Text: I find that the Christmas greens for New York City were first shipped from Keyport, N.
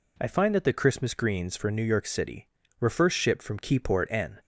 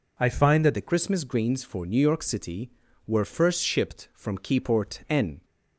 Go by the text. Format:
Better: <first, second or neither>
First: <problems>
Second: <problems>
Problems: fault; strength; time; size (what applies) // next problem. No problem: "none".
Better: first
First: none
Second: changes voice at "the"; from 0.7 s on; 4.7 s long